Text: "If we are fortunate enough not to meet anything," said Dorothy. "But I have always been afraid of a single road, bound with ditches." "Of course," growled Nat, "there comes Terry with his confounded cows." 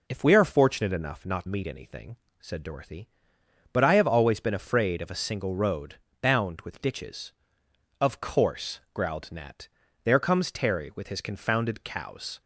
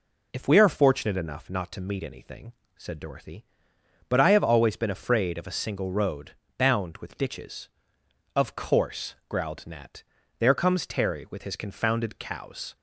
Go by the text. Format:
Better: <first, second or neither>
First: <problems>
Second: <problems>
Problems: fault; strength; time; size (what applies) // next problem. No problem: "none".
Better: second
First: skips "to"; at 1.4 s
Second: none